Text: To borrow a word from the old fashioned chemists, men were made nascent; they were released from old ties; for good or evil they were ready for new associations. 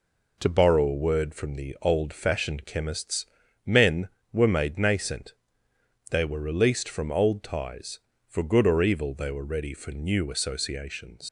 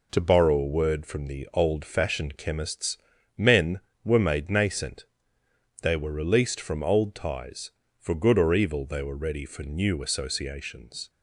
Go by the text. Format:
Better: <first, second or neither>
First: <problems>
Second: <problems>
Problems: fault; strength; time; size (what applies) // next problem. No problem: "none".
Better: second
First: leaves "associations" unfinished; at 11.2 s; 90 ms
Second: none